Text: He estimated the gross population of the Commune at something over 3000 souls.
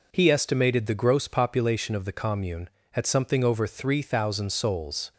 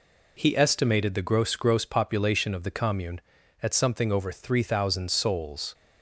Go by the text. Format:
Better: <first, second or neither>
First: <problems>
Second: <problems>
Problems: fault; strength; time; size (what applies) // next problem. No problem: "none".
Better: first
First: none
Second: says "gross" twice; at 1.5 s